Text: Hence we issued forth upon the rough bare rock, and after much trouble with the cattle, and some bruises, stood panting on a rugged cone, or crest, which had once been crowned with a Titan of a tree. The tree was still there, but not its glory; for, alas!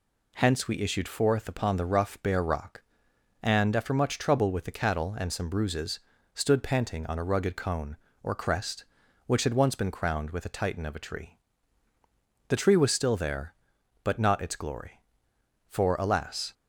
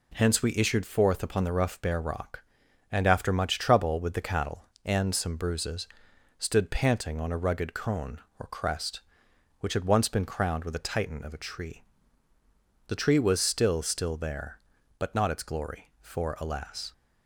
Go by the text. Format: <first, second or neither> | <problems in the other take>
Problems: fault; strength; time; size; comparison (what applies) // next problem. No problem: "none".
first | says "still" twice; at 13.8 s